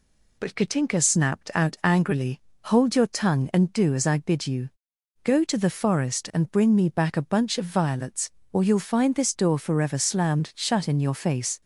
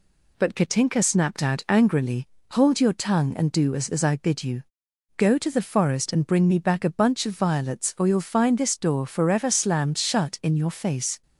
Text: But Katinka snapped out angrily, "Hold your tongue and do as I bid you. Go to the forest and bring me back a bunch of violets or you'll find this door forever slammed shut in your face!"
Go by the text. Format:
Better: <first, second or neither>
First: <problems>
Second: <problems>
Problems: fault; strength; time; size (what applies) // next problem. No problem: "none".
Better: first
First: none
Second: says "as" twice; at 3.8 s